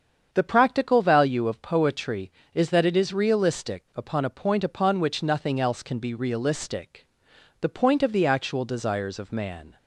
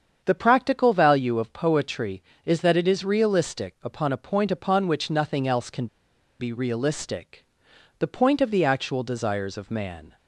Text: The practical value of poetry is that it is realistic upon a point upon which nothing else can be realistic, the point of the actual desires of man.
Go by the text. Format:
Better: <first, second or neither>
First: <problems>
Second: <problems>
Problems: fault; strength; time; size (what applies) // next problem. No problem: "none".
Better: first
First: starts louder than the rest; strong; until 1.3 s; 7.5 dB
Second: starts louder than the rest; strong; until 1.2 s; 7.5 dB // pauses between "can" and "be"; noticeable; at 5.8 s; 0.53 s long